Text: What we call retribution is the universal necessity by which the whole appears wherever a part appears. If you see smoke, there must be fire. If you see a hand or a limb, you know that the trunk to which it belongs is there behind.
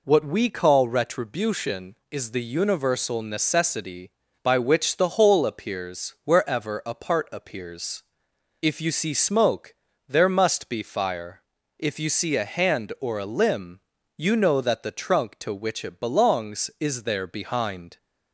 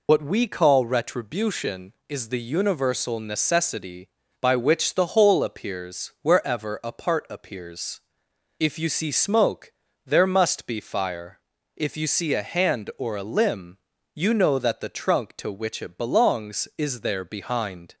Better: first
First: none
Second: loses the start of "What"; at 0.0 s; 55 ms

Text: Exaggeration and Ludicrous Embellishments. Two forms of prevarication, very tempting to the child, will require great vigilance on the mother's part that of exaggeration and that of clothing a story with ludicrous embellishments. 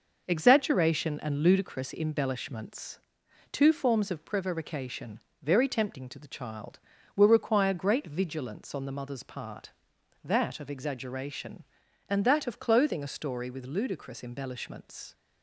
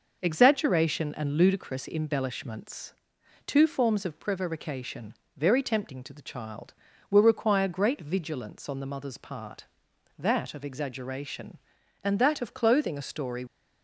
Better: first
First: none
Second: stops before "with ludicrous embellishments"; at 13.4 s

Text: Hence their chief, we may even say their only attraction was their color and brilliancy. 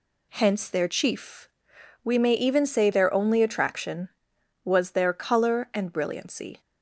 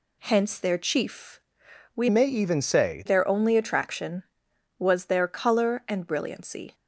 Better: first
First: none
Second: changes voice from "may" to "say"; from 2.0 to 3.0 s; 1.0 s long

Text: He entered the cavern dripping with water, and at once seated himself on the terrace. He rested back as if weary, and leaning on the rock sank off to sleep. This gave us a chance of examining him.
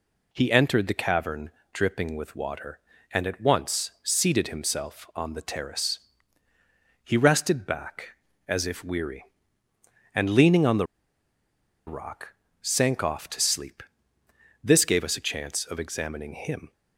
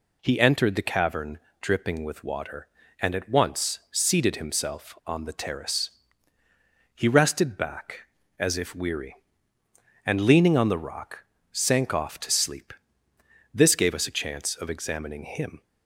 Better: second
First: pauses between "cavern" and "dripping"; slight; at 1.5 s; 0.24 s long // pauses between "the" and "rock"; at 10.8 s; 1.0 s long // pauses between "rock" and "sank"; slight; at 12.3 s; 0.28 s long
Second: pauses between "cavern" and "dripping"; slight; at 1.3 s; 0.24 s long // pauses between "rock" and "sank"; slight; at 11.2 s; 0.28 s long

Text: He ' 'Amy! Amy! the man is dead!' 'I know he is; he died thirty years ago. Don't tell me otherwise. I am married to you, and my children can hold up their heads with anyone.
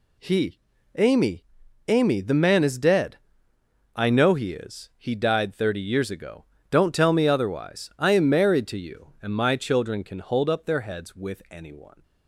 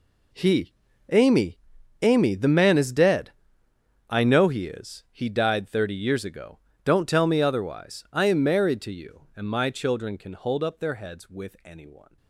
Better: first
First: none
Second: gets quieter; strong; throughout; 10.5 dB

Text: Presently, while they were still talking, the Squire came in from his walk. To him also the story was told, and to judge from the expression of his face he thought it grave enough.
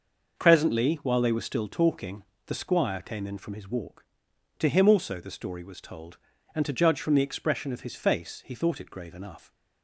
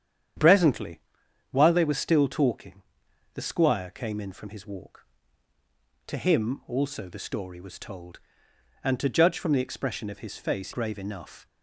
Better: first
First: none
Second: starts louder than the rest; strong; until 1.8 s; 9 dB // skips "he thought it"; at 10.7 s

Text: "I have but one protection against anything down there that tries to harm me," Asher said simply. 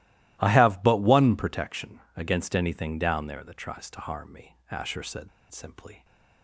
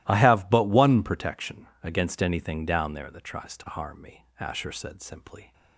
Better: second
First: starts louder than the rest; strong; until 1.4 s; 16 dB // pauses between "protection" and "against"; slight; at 1.9 s; 0.18 s long // pauses between "said" and "simply"; slight; at 5.2 s; 0.23 s long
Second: starts louder than the rest; strong; until 1.0 s; 16 dB // pauses between "protection" and "against"; slight; at 1.6 s; 0.18 s long

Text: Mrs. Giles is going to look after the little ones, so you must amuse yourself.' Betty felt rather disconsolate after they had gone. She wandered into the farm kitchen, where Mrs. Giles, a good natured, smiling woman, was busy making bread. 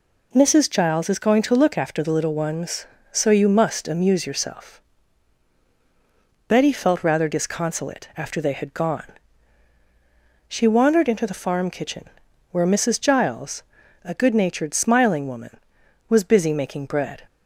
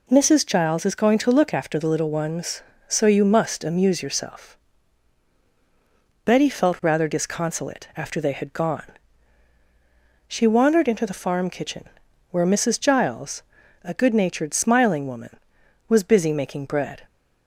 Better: neither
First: none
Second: none

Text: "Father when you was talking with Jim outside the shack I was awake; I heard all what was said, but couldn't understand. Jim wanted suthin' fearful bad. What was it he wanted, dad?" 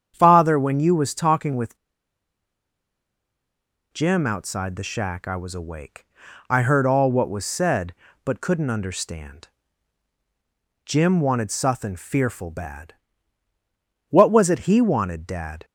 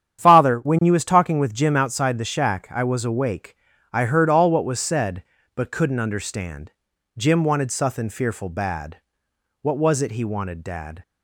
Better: second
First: starts louder than the rest; strong; until 1.1 s; 8 dB // pauses between "with" and "Jim"; strong; at 1.7 s; 2.1 s long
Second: starts louder than the rest; strong; until 1.2 s; 9 dB

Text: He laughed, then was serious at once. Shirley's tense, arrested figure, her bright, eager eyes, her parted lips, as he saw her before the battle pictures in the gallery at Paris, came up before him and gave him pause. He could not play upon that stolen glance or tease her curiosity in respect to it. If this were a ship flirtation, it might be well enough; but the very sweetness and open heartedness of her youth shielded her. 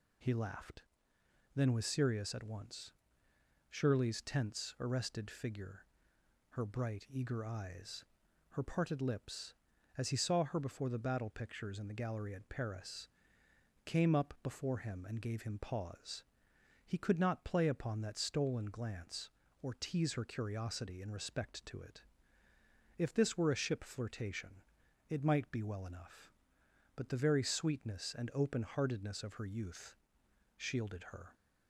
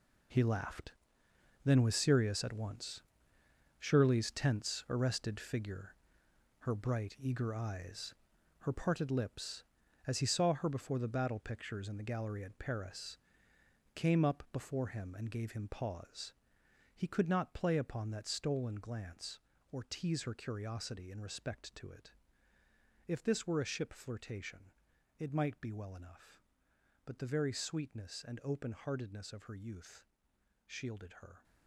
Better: first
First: pauses between "youth" and "shielded"; noticeable; at 29.9 s; 0.60 s long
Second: gets quieter; strong; throughout; 11.5 dB // pauses between "youth" and "shielded"; noticeable; at 30.0 s; 0.60 s long

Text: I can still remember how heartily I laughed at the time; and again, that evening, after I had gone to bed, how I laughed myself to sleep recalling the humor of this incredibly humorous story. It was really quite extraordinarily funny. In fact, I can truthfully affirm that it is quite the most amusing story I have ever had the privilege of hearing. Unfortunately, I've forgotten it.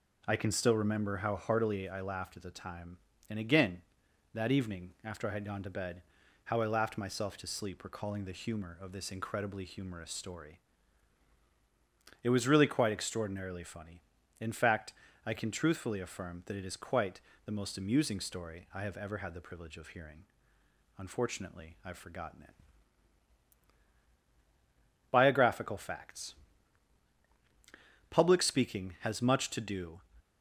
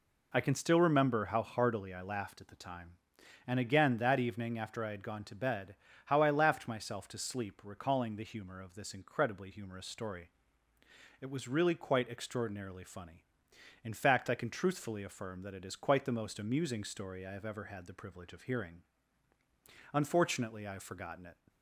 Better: second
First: pauses between "quite" and "the"; slight; at 17.1 s; 0.26 s long // goes on to say "Biographical Facts Public speaking has much to do"; strong; from 25.0 s on; 4.9 s long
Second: none

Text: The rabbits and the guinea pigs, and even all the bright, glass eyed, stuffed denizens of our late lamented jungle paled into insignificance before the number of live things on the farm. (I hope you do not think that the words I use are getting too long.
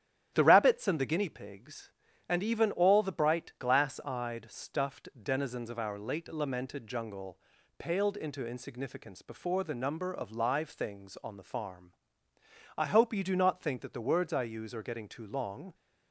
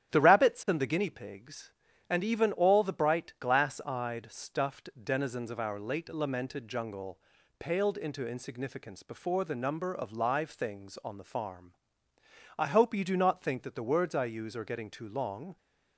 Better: neither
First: starts louder than the rest; strong; until 1.3 s; 11 dB // pauses between "jungle" and "paled"; at 7.3 s; 0.40 s long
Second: starts louder than the rest; strong; until 1.1 s; 11 dB // pauses between "jungle" and "paled"; at 7.1 s; 0.40 s long

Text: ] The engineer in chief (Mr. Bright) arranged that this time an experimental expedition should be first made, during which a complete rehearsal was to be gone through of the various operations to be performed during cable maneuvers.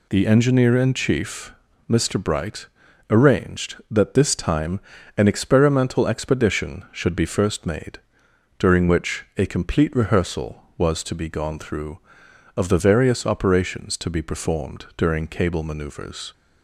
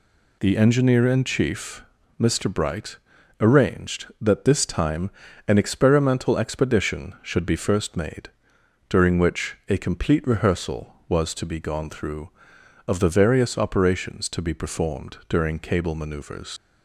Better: first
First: pauses between "time" and "an"; at 4.7 s; 0.38 s long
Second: pauses between "time" and "an"; at 5.0 s; 0.38 s long // leaves "maneuvers" unfinished; at 16.5 s; 75 ms

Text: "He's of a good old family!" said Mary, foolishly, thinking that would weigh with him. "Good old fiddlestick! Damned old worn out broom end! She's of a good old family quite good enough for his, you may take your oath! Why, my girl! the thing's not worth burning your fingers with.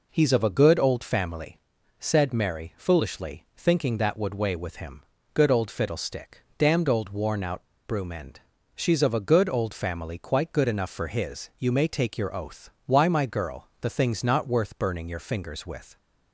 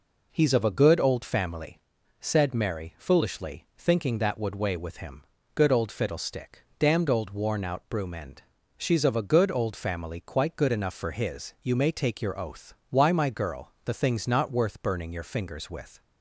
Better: second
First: pauses between "out" and "broom"; slight; at 7.6 s; 0.24 s long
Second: none

